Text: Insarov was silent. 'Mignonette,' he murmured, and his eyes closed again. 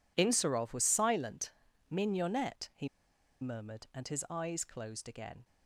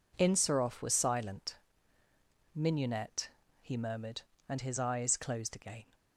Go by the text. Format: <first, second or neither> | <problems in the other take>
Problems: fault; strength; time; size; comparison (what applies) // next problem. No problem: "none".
second | pauses between "he" and "murmured"; noticeable; at 2.8 s; 0.53 s long